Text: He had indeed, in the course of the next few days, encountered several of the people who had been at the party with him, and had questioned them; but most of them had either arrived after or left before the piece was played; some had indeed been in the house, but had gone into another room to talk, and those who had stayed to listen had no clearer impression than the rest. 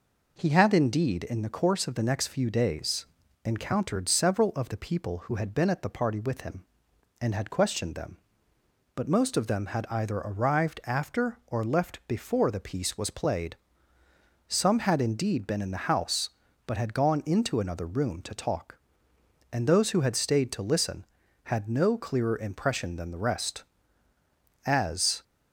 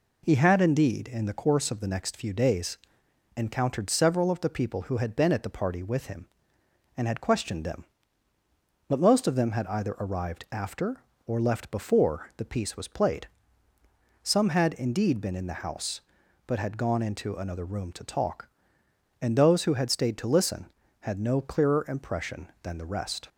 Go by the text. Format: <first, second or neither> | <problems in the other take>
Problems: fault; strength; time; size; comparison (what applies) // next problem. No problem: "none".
second | goes on to say "As"; from 24.6 s on; 0.56 s long